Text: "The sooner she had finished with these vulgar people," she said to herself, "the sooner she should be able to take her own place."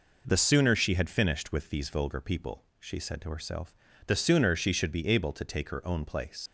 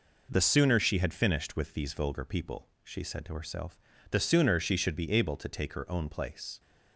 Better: second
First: leaves "place" unfinished; at 6.4 s; 100 ms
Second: none

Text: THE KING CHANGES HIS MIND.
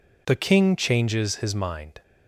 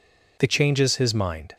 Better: first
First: none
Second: skips "KING"; at 0.4 s

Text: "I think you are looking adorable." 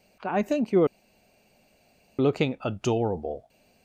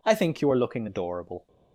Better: second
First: pauses between "are" and "looking"; strong; at 0.8 s; 1.3 s long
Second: none

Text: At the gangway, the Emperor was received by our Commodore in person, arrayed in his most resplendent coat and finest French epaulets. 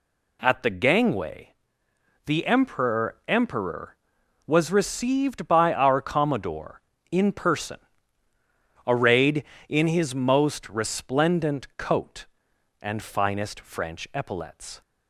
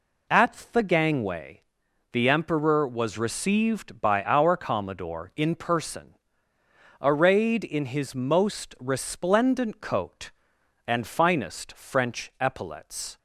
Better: second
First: says "Emperor" twice; at 3.2 s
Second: none

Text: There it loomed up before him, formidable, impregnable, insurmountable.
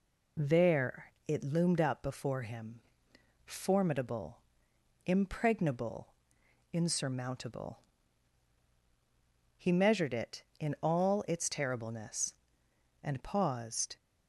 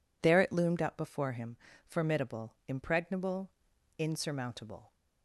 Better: second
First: pauses between "There" and "it"; slight; at 1.0 s; 0.20 s long // goes on to say "He measured it in all its terribleness and paused"; strong; from 9.5 s on; 4.4 s long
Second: none

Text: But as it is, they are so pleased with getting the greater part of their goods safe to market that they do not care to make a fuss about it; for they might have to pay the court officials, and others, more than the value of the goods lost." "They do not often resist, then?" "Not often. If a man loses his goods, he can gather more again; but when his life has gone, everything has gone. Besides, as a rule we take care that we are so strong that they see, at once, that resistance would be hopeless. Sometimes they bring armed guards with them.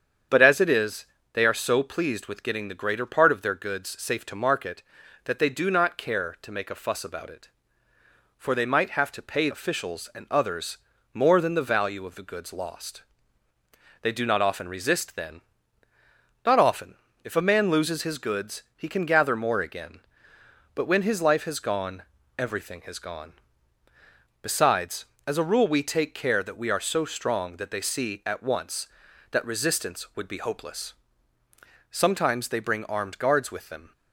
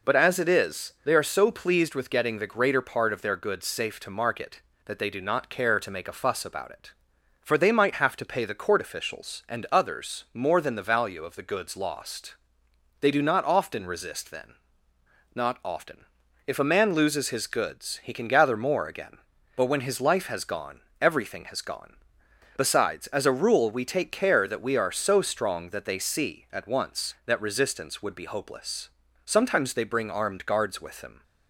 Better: second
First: starts louder than the rest; strong; until 1.5 s; 8 dB // skips "the court"; at 9.5 s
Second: none

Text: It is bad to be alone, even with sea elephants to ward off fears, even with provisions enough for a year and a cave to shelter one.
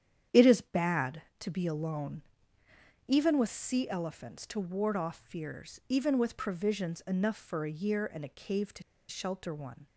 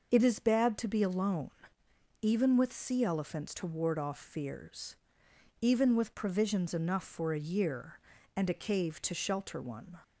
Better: second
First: starts louder than the rest; strong; until 1.5 s; 9.5 dB // pauses between "to" and "shelter"; slight; at 8.8 s; 0.27 s long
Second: none

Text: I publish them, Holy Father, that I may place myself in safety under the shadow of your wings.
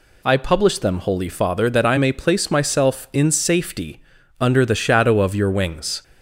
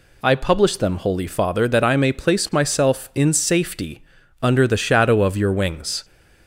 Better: neither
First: pauses between "safety" and "under"; slight; at 4.0 s; 0.36 s long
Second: pauses between "safety" and "under"; slight; at 4.0 s; 0.36 s long

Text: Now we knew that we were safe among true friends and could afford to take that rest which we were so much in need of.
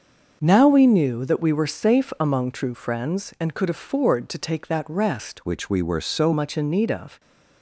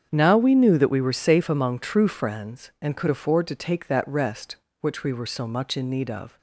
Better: second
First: starts louder than the rest; until 1.4 s; 6.5 dB // changes voice from "which" to "so"; from 5.4 to 6.3 s; 0.9 s long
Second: starts louder than the rest; strong; until 1.1 s; 7.5 dB

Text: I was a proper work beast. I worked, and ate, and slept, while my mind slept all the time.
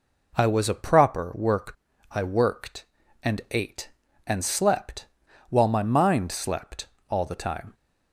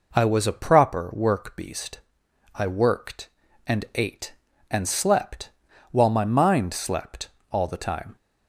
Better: second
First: skips "beast"; at 1.9 s // pauses between "slept" and "all"; slight; at 6.8 s; 0.24 s long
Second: pauses between "slept" and "all"; slight; at 7.2 s; 0.24 s long

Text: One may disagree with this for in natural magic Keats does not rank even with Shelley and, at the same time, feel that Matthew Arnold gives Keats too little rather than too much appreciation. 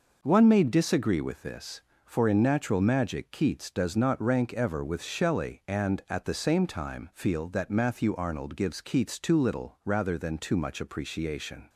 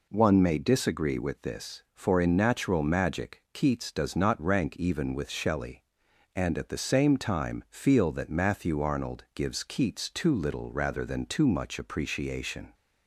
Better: second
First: says "ever" for "even"; at 4.5 s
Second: none

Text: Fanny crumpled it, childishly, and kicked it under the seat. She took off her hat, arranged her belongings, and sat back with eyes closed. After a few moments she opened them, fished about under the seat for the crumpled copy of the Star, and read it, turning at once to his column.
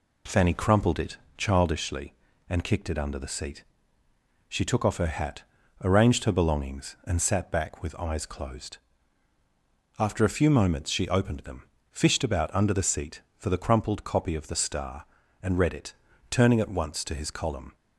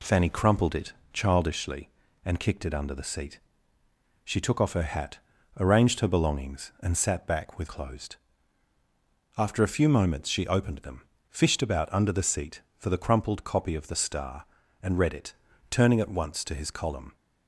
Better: first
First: none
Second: skips "eyes"; at 7.6 s

